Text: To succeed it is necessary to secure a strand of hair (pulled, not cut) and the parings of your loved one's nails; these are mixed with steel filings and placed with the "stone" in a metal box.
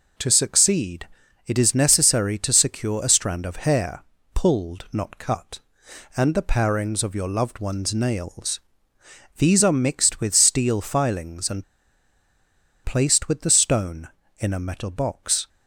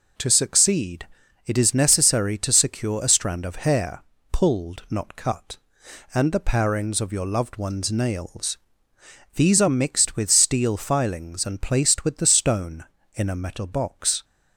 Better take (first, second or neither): second